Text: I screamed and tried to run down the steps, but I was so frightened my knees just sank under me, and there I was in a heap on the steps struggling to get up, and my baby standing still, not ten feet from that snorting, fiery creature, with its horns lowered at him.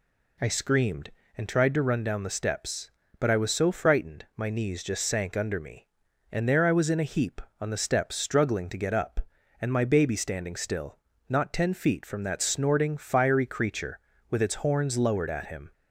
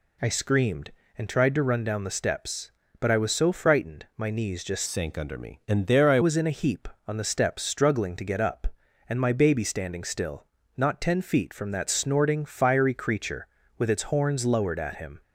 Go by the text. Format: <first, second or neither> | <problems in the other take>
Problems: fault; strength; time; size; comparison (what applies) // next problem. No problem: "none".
first | changes voice from "sank" to "I"; from 4.8 to 6.1 s; 1.3 s long